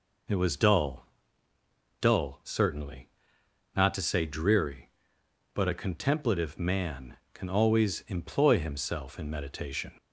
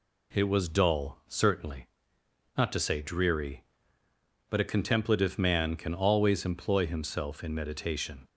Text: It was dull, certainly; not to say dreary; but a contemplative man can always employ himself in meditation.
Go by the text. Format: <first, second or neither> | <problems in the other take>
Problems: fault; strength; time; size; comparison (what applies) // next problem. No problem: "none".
second | says "dull" twice; at 2.0 s